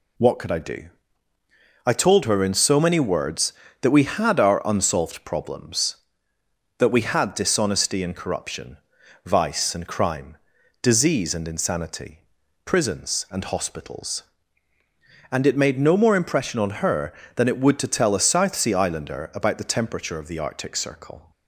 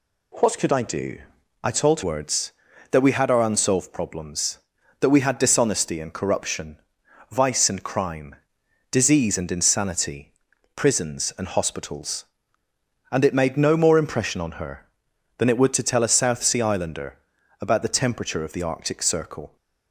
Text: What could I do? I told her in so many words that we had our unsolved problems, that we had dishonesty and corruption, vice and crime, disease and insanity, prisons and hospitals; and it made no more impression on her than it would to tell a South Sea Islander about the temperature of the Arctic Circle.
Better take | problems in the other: first | skips "her in so many"; at 2.0 s // pauses between "Islander" and "about"; at 17.1 s; 0.42 s long

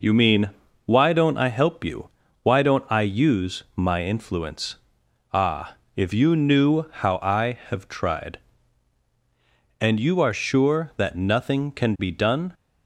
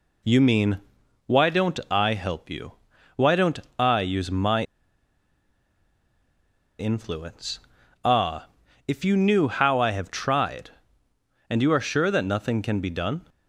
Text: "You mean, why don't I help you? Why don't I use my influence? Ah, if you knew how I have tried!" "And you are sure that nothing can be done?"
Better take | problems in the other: first | pauses between "don't" and "I"; slight; at 3.5 s; 0.18 s long // pauses between "my" and "influence"; strong; at 4.6 s; 2.1 s long

